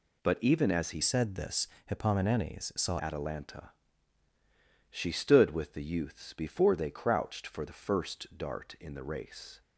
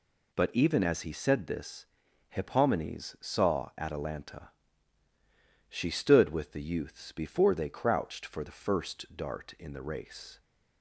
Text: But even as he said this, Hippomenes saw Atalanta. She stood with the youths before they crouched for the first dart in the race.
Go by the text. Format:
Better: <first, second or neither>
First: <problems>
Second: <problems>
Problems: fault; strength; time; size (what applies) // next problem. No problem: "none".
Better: second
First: changes voice from "said" to "saw"; from 1.0 to 2.9 s; 1.9 s long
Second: none